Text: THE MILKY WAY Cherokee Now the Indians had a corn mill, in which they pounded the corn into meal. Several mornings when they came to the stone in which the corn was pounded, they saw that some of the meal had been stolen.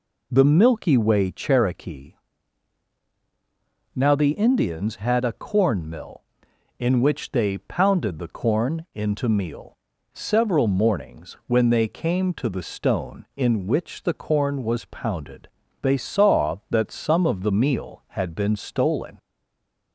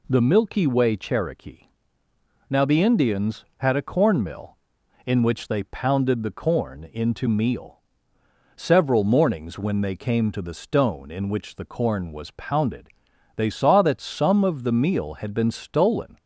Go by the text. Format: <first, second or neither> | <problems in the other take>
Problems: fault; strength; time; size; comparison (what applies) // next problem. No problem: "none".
second | pauses between "Cherokee" and "Now"; strong; at 2.1 s; 1.8 s long; noticeable in the second // stays silent after the last word; slight; from 19.1 s on; 0.8 s long